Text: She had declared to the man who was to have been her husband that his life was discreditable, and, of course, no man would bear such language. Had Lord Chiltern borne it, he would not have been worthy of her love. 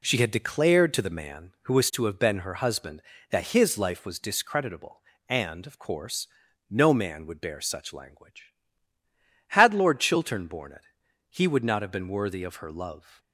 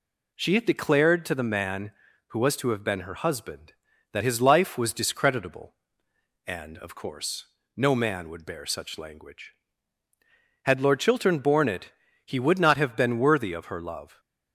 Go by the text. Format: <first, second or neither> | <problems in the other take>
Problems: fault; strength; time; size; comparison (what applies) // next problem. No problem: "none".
neither | none